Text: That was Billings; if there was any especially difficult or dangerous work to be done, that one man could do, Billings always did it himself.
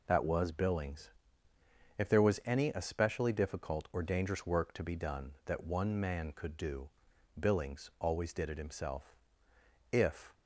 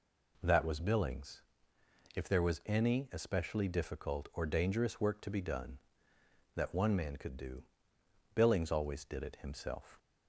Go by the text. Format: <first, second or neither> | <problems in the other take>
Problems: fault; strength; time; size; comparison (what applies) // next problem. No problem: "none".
second | goes on to say "If"; slight; from 9.9 s on; 0.40 s long